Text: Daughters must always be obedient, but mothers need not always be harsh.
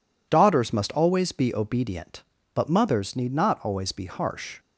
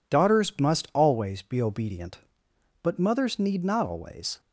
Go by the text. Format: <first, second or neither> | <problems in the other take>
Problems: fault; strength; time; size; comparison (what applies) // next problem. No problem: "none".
first | stops before "be harsh"; at 4.3 s